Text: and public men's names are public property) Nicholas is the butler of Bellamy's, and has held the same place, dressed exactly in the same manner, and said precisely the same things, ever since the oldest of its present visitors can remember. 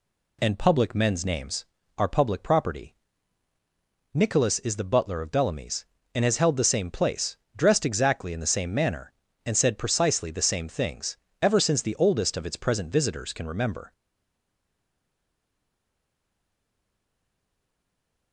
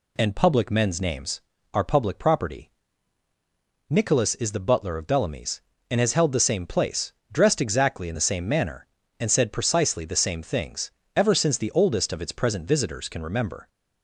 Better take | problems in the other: second | stays silent after the last word; strong; from 13.9 s on; 4.4 s long

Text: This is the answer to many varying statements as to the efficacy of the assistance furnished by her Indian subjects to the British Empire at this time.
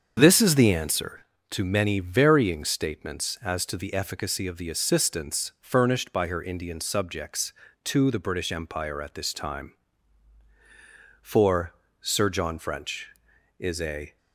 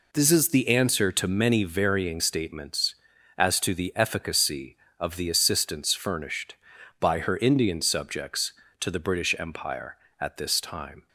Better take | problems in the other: second | starts louder than the rest; until 1.1 s; 7 dB // goes on to say "For Sir John French is a"; strong; from 11.2 s on; 2.9 s long

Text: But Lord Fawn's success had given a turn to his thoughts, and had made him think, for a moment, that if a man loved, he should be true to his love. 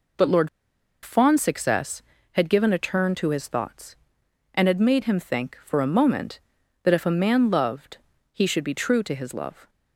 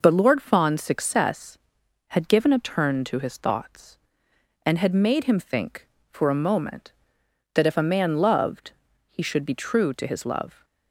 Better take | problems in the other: second | pauses between "Lord" and "Fawn's"; noticeable; at 0.4 s; 0.54 s long

